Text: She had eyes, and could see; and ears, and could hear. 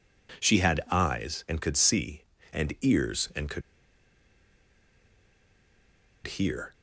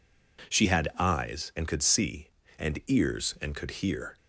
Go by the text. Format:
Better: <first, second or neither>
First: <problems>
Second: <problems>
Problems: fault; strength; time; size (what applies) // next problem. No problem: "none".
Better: second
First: pauses between "could" and "hear"; strong; at 3.6 s; 2.6 s long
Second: none